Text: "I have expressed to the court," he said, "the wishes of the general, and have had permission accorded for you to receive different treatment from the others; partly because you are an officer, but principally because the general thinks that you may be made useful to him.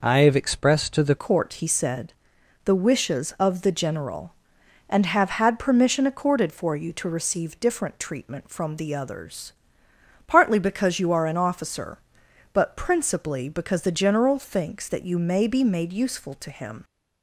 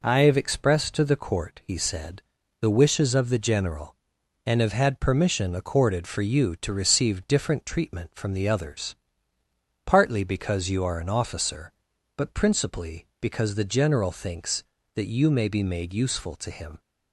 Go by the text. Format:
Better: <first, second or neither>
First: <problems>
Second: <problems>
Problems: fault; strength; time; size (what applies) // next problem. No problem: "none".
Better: second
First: changes voice at "court"; from 1.1 s on; 15.7 s long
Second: none